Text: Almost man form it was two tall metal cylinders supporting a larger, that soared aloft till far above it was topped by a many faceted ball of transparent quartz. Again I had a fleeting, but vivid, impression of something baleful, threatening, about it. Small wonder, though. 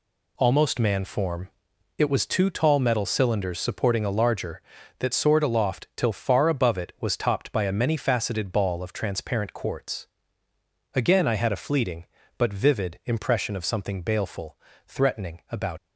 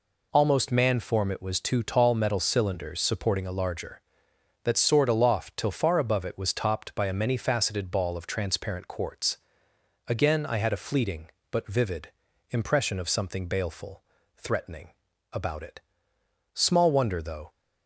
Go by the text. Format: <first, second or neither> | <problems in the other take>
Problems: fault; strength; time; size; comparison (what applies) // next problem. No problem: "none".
second | pauses between "form" and "it"; noticeable; at 1.4 s; 0.48 s long // stops before "it Small wonder though"; at 15.7 s